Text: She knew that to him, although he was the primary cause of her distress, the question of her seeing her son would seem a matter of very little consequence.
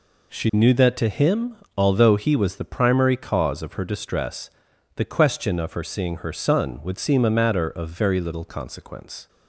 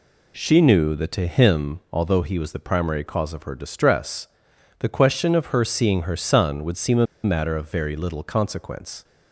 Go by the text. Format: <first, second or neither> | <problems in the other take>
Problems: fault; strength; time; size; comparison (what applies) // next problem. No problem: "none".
first | pauses between "a" and "matter"; slight; at 7.0 s; 0.18 s long